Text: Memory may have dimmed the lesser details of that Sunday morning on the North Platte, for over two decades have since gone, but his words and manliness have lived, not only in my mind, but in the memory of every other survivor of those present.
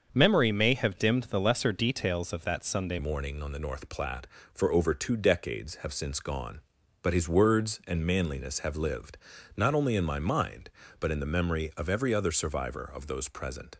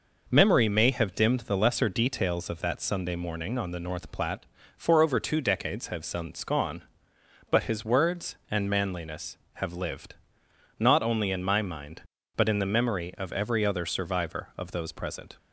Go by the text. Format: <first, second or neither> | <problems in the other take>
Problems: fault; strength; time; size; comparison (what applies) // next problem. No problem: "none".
second | starts louder than the rest; until 1.1 s; 6.5 dB // changes voice at "morning"; from 2.9 s on; 10.8 s long